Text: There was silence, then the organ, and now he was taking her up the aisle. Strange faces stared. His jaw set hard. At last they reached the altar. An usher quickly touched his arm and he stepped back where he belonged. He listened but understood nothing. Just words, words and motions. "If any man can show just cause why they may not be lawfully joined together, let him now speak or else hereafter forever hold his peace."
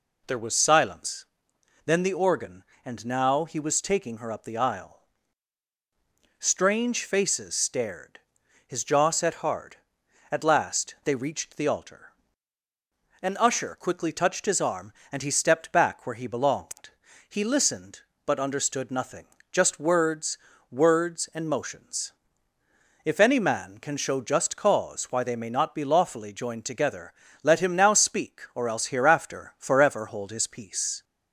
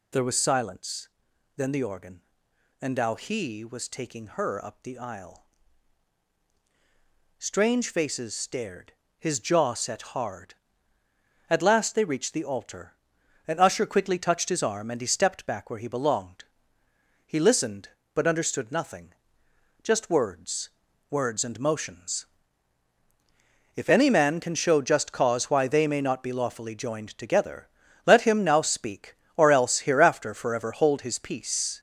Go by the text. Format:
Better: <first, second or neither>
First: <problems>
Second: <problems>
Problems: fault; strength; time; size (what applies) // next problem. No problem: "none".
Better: first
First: none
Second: gets louder; noticeable; throughout; 5.5 dB